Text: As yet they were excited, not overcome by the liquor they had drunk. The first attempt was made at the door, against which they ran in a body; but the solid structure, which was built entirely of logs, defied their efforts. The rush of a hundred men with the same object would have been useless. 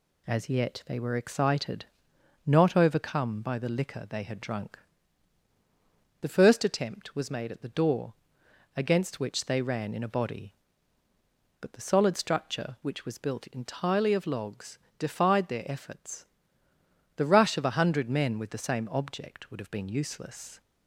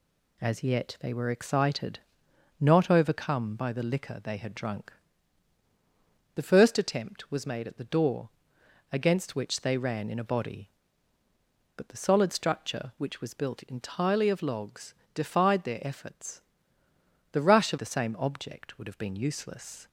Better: first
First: none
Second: skips "a hundred men with"; at 17.7 s

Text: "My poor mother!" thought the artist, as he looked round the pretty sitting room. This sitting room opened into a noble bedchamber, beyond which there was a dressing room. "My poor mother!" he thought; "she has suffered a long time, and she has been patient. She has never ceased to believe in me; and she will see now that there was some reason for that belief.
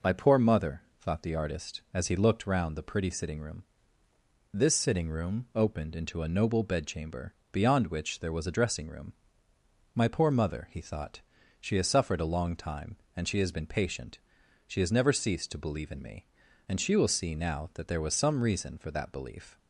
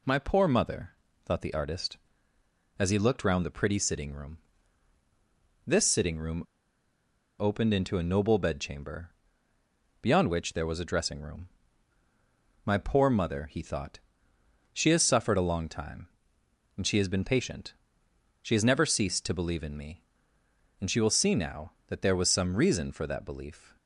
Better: first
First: none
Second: pauses between "room" and "opened"; noticeable; at 6.4 s; 0.95 s long

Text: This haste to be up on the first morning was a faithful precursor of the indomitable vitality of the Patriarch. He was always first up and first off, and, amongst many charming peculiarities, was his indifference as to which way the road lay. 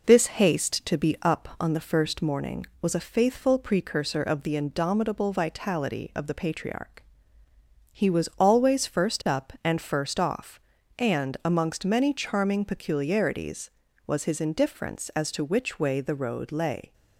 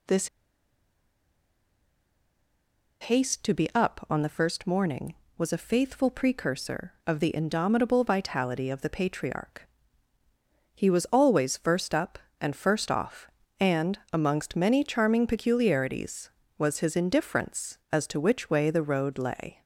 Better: first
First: none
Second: pauses between "This" and "haste"; strong; at 0.2 s; 2.7 s long

